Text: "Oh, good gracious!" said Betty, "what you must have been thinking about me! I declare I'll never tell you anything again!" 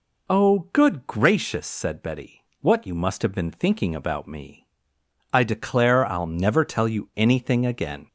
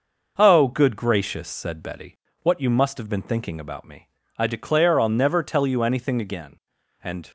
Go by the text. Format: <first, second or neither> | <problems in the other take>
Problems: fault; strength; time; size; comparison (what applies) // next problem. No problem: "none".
first | goes on to say "and"; slight; from 7.0 s on; 0.26 s long